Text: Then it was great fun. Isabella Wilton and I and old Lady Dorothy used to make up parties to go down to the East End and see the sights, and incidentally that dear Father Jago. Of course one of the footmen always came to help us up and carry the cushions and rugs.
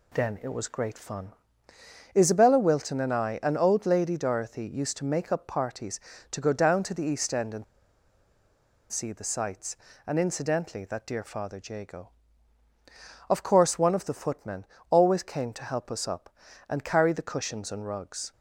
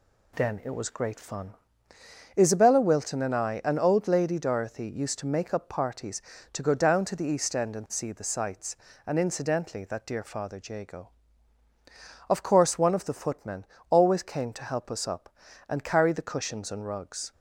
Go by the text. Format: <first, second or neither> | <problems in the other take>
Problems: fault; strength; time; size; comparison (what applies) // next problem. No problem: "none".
second | pauses between "and" and "see"; strong; at 7.6 s; 1.2 s long // pauses between "footmen" and "always"; slight; at 14.6 s; 0.24 s long; slight in the second